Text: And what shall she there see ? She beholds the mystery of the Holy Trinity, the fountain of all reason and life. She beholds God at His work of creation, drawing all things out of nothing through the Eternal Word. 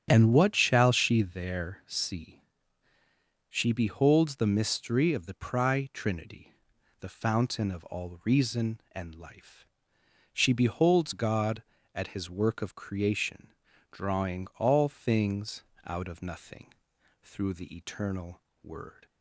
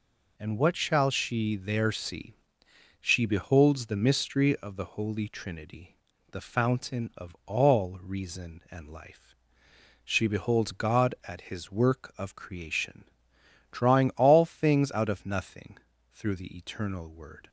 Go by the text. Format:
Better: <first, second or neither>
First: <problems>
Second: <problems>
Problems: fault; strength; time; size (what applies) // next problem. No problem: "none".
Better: second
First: starts louder than the rest; strong; until 1.1 s; 8.5 dB // says "Pri" for "Holy"; at 5.3 s // pauses between "things" and "out"; slight; at 15.6 s; 0.22 s long // pauses between "nothing" and "through"; noticeable; at 16.7 s; 0.48 s long // pauses between "Eternal" and "Word"; slight; at 18.3 s; 0.24 s long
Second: pauses between "nothing" and "through"; slight; at 15.7 s; 0.34 s long